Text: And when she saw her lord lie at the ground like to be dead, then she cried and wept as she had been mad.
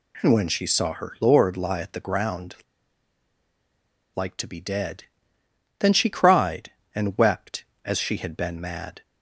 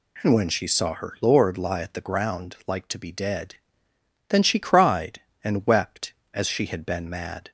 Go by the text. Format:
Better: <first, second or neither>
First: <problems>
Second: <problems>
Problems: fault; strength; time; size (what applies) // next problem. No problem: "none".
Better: second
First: pauses between "ground" and "like"; strong; at 2.5 s; 1.5 s long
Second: none